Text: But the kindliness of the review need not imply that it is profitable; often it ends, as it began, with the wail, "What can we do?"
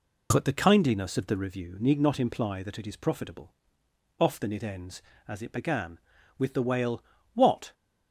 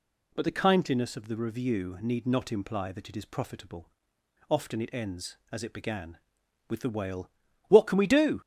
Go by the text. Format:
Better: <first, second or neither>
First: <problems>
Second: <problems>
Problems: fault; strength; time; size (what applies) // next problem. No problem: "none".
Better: second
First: stops before "can we do"; at 7.7 s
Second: none